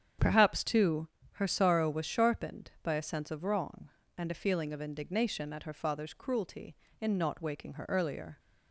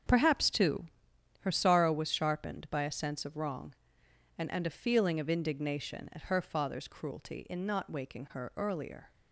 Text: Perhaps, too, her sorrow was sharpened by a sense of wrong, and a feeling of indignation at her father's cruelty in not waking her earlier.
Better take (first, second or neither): first